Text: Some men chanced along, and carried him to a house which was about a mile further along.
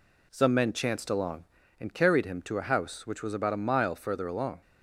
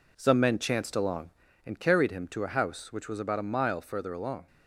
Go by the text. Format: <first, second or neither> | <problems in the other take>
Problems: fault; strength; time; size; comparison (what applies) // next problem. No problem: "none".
first | gets quieter; throughout; 6 dB